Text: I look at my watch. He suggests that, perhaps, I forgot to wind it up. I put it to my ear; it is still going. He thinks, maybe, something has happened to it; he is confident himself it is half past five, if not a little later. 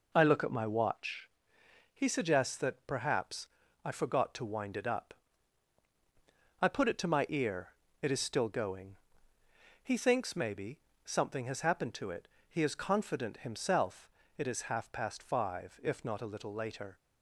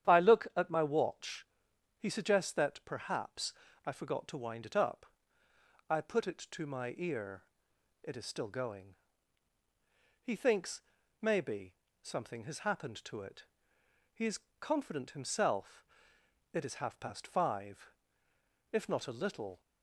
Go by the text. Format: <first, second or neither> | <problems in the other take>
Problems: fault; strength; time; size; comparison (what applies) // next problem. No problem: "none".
first | starts louder than the rest; strong; until 1.1 s; 10 dB // pauses between "is" and "confident"; slight; at 14.3 s; 0.22 s long // pauses between "himself" and "it"; noticeable; at 15.8 s; 0.70 s long; slight in the first // stops before "later"; at 19.5 s